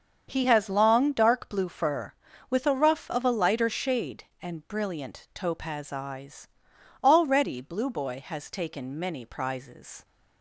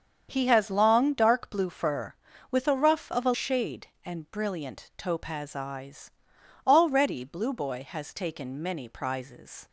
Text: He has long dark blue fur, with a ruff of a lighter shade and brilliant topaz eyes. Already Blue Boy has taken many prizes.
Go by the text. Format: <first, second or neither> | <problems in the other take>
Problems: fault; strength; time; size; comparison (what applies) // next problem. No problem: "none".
first | starts louder than the rest; strong; until 1.3 s; 7 dB; also in the first // skips "lighter"; at 3.3 s